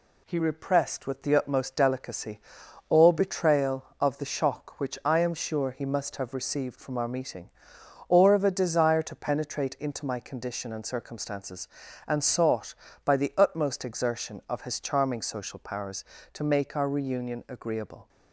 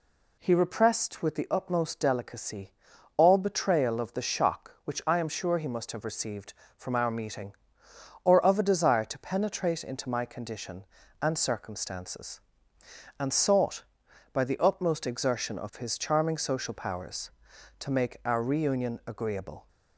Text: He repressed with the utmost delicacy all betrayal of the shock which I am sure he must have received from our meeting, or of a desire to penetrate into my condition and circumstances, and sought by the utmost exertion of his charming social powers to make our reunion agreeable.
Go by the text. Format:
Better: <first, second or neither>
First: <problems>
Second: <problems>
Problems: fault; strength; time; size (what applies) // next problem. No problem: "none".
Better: neither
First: pauses between "delicacy" and "all"; noticeable; at 2.3 s; 0.50 s long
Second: pauses between "delicacy" and "all"; at 2.7 s; 0.44 s long